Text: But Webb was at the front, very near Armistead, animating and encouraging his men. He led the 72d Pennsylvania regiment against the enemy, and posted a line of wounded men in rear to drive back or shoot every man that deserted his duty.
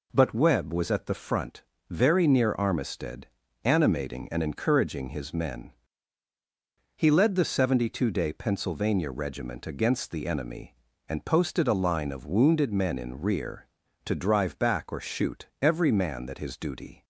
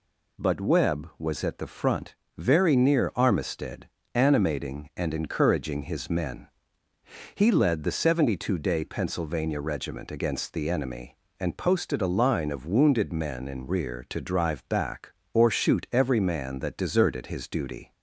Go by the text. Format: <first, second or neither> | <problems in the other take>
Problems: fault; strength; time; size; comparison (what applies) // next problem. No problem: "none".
second | pauses between "shoot" and "every"; slight; at 15.4 s; 0.16 s long // skips "deserted"; at 16.3 s